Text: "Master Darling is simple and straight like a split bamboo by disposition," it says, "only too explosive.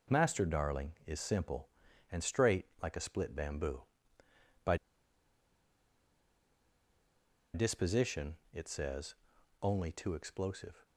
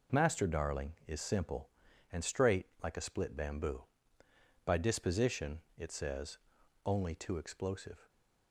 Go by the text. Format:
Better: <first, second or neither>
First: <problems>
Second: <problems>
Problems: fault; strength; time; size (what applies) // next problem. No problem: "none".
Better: second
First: pauses between "straight" and "like"; slight; at 2.6 s; 0.16 s long // pauses between "by" and "disposition"; strong; at 4.7 s; 2.7 s long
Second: pauses between "straight" and "like"; slight; at 2.6 s; 0.16 s long